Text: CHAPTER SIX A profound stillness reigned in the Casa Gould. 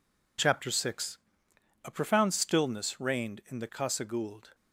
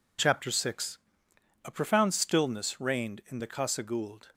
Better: neither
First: pauses between "SIX" and "A"; noticeable; at 1.1 s; 0.66 s long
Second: pauses between "SIX" and "A"; noticeable; at 0.9 s; 0.66 s long

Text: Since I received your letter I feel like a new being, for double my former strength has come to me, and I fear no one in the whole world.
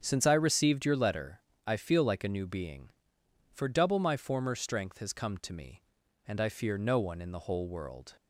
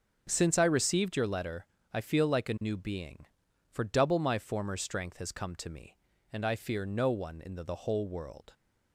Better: first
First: starts louder than the rest; strong; until 1.0 s; 7.5 dB // pauses between "letter" and "I"; slight; at 1.4 s; 0.22 s long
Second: starts louder than the rest; until 1.3 s; 7 dB // pauses between "letter" and "I"; slight; at 1.6 s; 0.30 s long // says "the" twice; at 7.6 s

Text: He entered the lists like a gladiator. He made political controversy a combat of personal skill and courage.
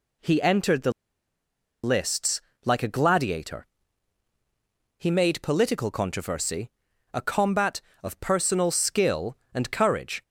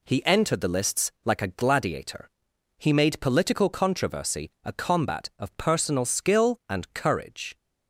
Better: second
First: pauses between "the" and "lists"; noticeable; at 0.9 s; 0.92 s long // pauses between "lists" and "like"; slight; at 2.3 s; 0.24 s long // pauses between "controversy" and "a"; at 6.6 s; 0.42 s long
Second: pauses between "controversy" and "a"; slight; at 4.4 s; 0.16 s long

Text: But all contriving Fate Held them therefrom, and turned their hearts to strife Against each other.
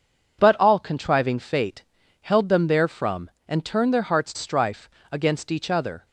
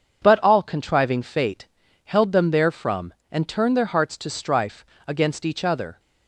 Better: second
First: pauses between "Fate" and "Held"; at 1.8 s; 0.38 s long // skips "to"; at 4.3 s // pauses between "strife" and "Against"; slight; at 4.8 s; 0.20 s long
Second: pauses between "Fate" and "Held"; at 1.6 s; 0.38 s long // pauses between "strife" and "Against"; slight; at 4.8 s; 0.20 s long

